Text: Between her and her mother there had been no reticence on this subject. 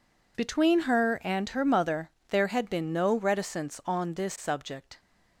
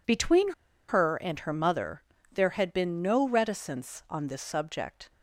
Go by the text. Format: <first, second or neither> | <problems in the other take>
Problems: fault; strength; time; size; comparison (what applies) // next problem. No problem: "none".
first | pauses between "Between" and "her"; at 0.5 s; 0.37 s long // pauses between "mother" and "there"; slight; at 2.0 s; 0.30 s long; slight in the first